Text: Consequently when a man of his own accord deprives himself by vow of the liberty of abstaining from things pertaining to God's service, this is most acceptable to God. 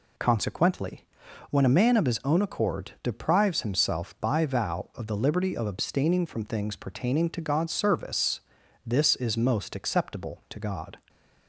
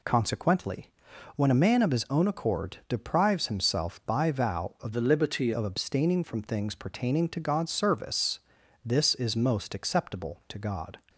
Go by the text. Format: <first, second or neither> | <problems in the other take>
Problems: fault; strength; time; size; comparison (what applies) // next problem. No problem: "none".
first | pauses between "Consequently" and "when"; noticeable; at 0.8 s; 0.46 s long; noticeable in the first // changes voice from "the" to "liberty"; from 4.9 to 5.5 s; 0.6 s long